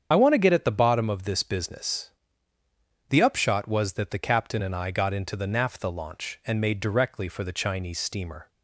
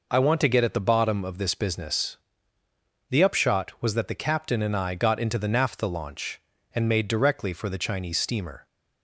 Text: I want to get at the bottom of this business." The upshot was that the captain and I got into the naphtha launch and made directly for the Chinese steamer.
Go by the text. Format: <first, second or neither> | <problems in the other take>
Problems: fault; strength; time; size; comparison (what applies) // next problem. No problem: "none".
second | loses the start of "I"; at 0.1 s; 45 ms // starts louder than the rest; strong; until 1.1 s; 8 dB